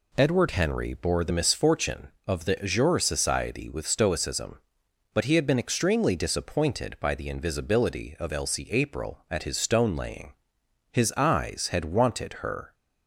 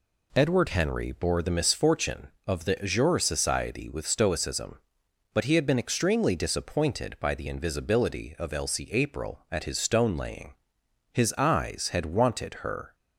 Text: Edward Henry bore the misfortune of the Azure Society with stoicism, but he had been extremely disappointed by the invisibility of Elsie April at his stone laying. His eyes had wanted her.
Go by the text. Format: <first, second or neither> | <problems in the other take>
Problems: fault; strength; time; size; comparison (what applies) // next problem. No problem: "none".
neither | none